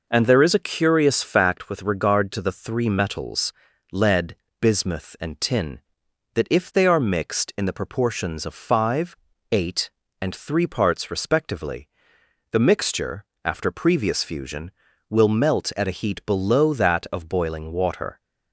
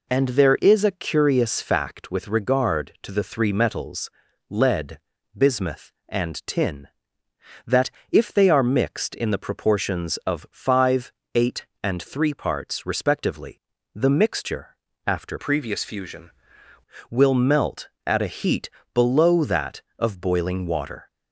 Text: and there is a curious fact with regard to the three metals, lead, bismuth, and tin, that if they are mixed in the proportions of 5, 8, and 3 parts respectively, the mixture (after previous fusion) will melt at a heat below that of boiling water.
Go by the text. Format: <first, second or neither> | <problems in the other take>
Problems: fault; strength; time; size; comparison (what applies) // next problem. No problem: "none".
first | pauses between "that" and "if"; slight; at 7.8 s; 0.22 s long // changes voice from "previous" to "fusion"; from 15.3 to 16.3 s; 1.0 s long // pauses between "heat" and "below"; slight; at 18.6 s; 0.24 s long